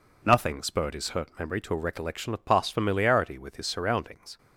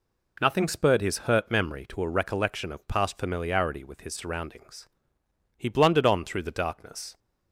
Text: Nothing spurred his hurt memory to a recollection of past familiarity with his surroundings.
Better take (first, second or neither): first